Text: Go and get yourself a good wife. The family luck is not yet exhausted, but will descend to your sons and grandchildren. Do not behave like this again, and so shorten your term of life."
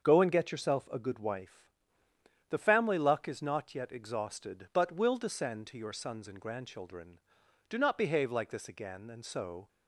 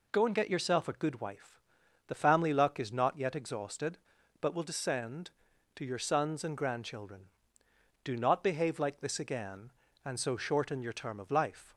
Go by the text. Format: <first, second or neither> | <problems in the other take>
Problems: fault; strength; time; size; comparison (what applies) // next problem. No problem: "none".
second | starts louder than the rest; until 1.0 s; 6.5 dB // stops before "shorten your term of life"; at 9.6 s